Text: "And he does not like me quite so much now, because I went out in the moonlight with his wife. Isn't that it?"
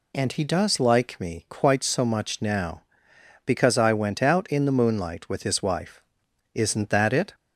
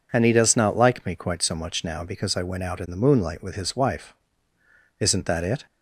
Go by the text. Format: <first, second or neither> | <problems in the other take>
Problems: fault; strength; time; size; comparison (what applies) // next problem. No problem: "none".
second | skips "not"; at 0.8 s